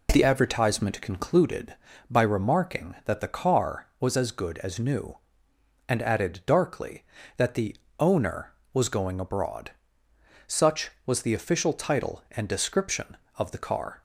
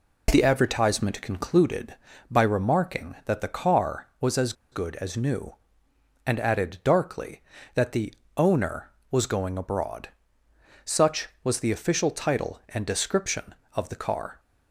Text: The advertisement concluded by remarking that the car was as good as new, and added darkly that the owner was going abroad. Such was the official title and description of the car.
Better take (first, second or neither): first